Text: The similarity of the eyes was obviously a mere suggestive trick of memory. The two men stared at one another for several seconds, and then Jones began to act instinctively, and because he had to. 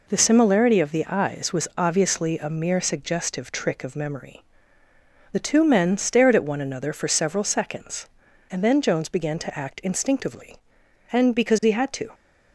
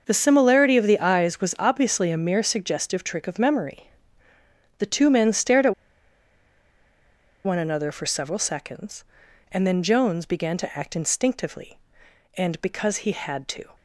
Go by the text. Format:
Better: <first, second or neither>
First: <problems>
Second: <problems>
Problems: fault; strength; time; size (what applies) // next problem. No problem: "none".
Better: first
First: none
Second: starts louder than the rest; until 1.0 s; 6 dB // pauses between "at" and "one"; strong; at 5.7 s; 1.7 s long